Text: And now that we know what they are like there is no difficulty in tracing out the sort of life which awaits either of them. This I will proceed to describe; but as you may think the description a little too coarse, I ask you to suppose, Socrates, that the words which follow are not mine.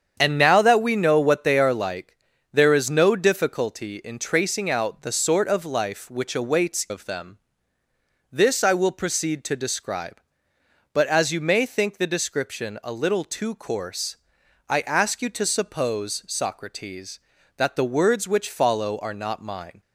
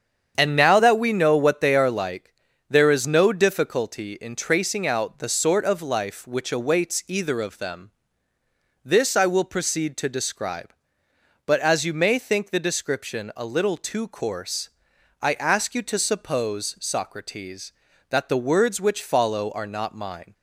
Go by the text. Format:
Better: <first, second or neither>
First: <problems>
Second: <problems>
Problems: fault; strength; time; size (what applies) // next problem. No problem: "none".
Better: second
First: starts louder than the rest; strong; until 1.1 s; 8 dB // pauses between "like" and "there"; at 2.1 s; 0.38 s long // skips "either"; at 6.8 s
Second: starts louder than the rest; strong; until 1.3 s; 7.5 dB // pauses between "like" and "there"; at 2.3 s; 0.38 s long